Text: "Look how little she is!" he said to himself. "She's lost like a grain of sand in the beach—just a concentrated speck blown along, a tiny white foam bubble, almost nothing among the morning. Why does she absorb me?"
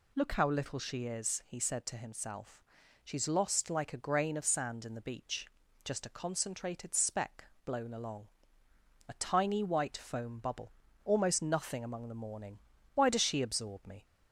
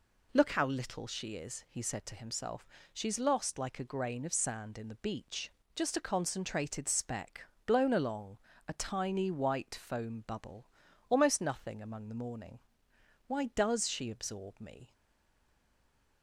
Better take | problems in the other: first | pauses between "speck" and "blown"; slight; at 7.4 s; 0.20 s long; slight in the first // stays silent after the last word; noticeable; from 14.9 s on; 1.3 s long

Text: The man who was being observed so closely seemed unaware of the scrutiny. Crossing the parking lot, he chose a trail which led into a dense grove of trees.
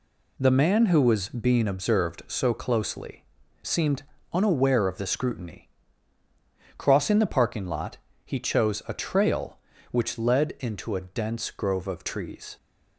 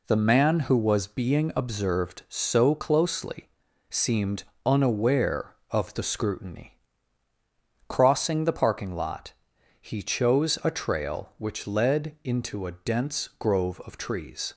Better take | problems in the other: neither | pauses between "closely" and "seemed"; the same in both // pauses between "seemed" and "unaware"; slight; the same in both

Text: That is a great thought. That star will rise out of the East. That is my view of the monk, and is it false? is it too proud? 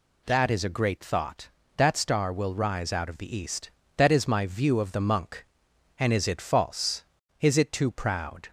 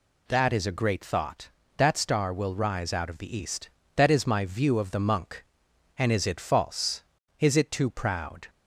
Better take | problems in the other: neither | none

